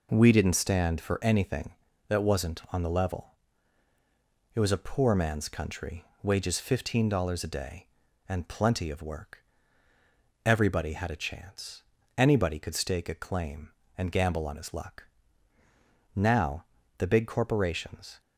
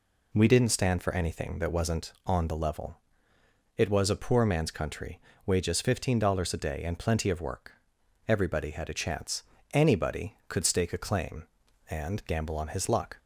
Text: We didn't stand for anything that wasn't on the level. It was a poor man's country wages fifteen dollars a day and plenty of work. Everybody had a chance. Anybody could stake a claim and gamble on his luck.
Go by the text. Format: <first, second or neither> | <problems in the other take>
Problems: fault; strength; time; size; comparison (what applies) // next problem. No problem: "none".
second | pauses between "country" and "wages"; slight; at 6.0 s; 0.20 s long; slight in the second // goes on to say "Now the big corporations"; strong; from 16.1 s on; 2.0 s long